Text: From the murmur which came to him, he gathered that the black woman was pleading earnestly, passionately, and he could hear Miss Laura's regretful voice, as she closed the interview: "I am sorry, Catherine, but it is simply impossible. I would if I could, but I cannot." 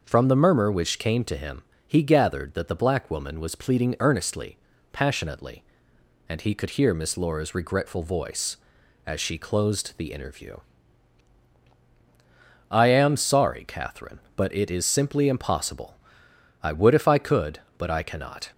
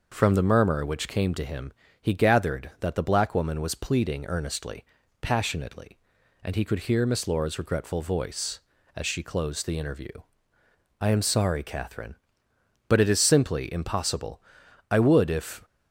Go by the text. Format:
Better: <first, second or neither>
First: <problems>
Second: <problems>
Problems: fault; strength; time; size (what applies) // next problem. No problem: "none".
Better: first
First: none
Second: stops before "I could but I cannot"; at 15.6 s